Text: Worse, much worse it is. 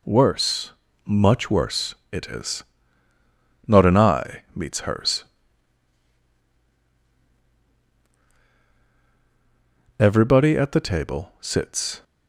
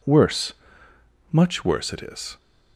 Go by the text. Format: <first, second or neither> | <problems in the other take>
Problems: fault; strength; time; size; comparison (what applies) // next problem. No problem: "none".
second | pauses between "worse" and "it"; slight; at 1.9 s; 0.16 s long // goes on to say "Not an eye meets hers Everybody at the table sits"; strong; from 3.6 s on; 8.3 s long